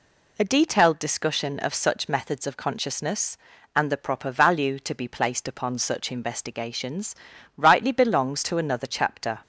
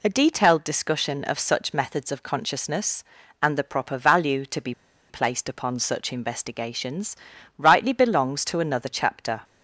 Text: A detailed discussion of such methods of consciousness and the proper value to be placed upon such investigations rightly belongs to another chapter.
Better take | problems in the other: first | pauses between "be" and "placed"; at 4.7 s; 0.36 s long // pauses between "investigations" and "rightly"; at 7.1 s; 0.42 s long; also in the first

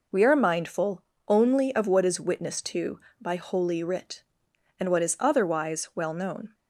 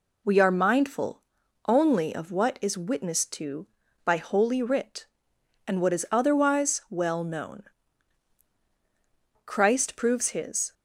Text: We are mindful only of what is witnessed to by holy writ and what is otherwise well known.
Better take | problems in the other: first | pauses between "mindful" and "only"; noticeable; at 1.2 s; 0.46 s long; slight in the first // goes on to say "Christ proves His"; noticeable; from 9.4 s on; 1.2 s long

